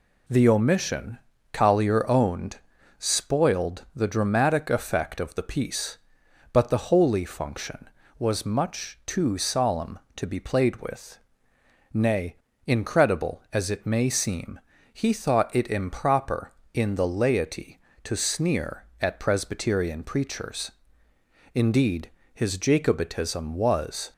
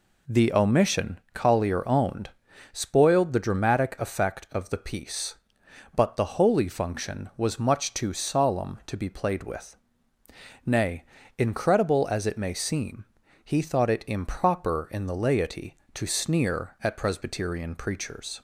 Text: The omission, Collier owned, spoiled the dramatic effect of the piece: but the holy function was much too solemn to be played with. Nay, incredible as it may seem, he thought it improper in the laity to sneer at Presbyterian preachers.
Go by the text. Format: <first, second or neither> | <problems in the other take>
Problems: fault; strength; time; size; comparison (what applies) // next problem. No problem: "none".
second | goes on to say "Indeed his Jacobitism was"; strong; from 21.5 s on; 2.5 s long